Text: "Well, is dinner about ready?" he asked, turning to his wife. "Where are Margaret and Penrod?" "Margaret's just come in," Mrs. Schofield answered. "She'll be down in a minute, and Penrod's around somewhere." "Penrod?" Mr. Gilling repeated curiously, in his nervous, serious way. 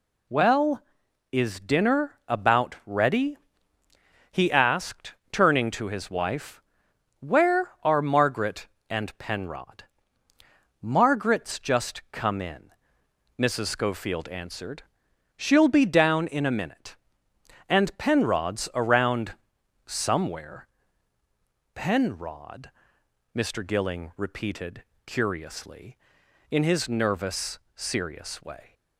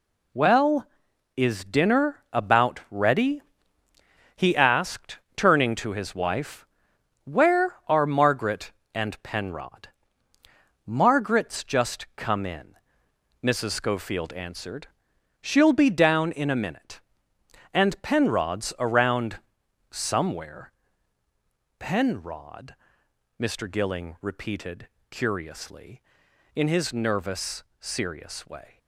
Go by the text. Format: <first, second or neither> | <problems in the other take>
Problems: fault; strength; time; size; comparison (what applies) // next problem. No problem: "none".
first | gets quieter; strong; throughout; 7.5 dB // pauses between "around" and "somewhere"; noticeable; at 19.3 s; 0.50 s long; noticeable in the first // pauses between "repeated" and "curiously"; slight; at 24.8 s; 0.22 s long; slight in the first